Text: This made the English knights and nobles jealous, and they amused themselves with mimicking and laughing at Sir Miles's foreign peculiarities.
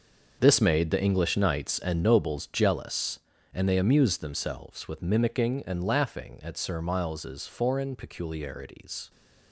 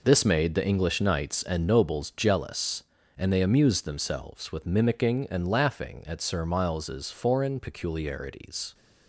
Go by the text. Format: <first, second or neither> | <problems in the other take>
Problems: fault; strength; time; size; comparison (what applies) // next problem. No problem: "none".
second | gets quieter; strong; throughout; 11 dB